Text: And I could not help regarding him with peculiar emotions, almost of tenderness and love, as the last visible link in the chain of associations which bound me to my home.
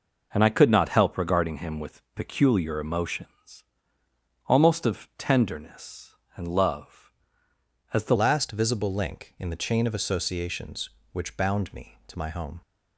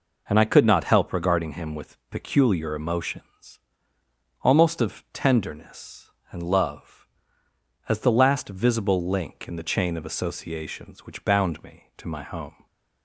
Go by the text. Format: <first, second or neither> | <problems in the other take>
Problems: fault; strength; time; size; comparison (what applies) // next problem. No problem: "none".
second | changes voice at "last"; from 8.1 s on; 4.5 s long